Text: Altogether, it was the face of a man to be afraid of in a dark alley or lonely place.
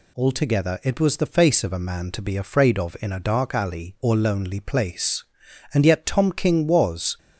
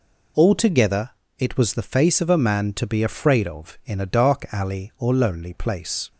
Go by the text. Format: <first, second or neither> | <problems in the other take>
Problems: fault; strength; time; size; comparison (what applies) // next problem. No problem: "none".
second | goes on to say "And yet Tom King was"; from 5.7 s on; 1.4 s long